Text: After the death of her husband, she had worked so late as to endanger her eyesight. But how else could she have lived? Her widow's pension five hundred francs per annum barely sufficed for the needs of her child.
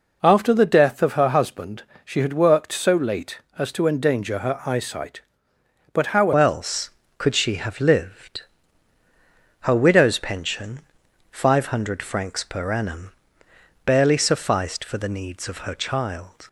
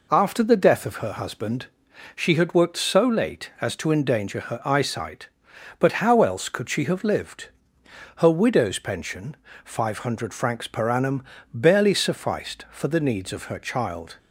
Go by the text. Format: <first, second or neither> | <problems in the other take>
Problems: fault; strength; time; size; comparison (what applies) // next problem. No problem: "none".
second | changes voice at "else"; from 6.3 s on; 10.1 s long // pauses between "pension" and "five"; noticeable; at 10.7 s; 0.52 s long; slight in the second // pauses between "annum" and "barely"; noticeable; at 13.1 s; 0.74 s long; slight in the second